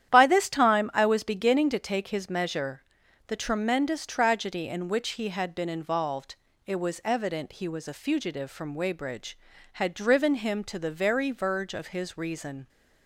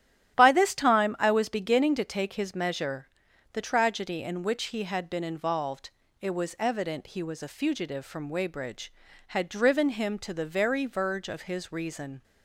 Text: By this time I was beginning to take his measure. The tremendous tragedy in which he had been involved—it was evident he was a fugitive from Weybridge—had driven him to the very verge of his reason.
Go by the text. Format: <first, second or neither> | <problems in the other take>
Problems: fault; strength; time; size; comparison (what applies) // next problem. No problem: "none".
first | starts louder than the rest; strong; until 1.3 s; 12 dB; strong in the first // skips "tremendous"; at 3.6 s